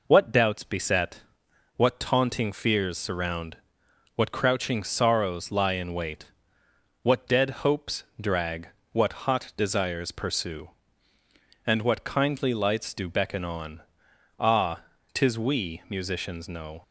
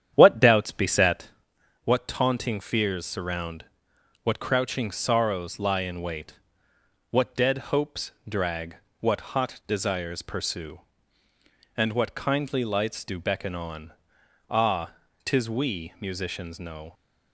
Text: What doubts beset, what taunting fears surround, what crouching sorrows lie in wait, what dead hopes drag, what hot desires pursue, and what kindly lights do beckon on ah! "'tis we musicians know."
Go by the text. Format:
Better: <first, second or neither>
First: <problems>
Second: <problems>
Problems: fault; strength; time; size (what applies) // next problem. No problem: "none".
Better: first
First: pauses between "dead" and "hopes"; slight; at 7.4 s; 0.16 s long // pauses between "hopes" and "drag"; slight; at 8.0 s; 0.18 s long // pauses between "on" and "ah"; noticeable; at 13.8 s; 0.58 s long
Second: starts louder than the rest; strong; until 1.4 s; 9.5 dB // pauses between "dead" and "hopes"; slight; at 7.5 s; 0.16 s long // pauses between "hopes" and "drag"; slight; at 8.1 s; 0.18 s long // pauses between "on" and "ah"; noticeable; at 13.9 s; 0.58 s long